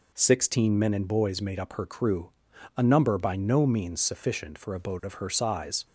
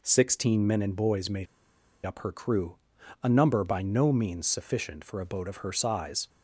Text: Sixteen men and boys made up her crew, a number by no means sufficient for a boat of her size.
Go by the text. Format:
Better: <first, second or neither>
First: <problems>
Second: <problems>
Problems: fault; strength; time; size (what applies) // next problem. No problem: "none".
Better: first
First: none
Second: pauses between "made" and "up"; noticeable; at 1.4 s; 0.60 s long